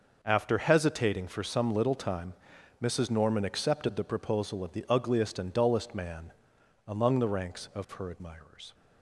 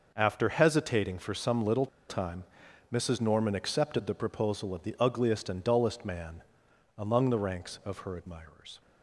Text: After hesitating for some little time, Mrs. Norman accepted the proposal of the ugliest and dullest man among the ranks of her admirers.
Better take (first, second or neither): first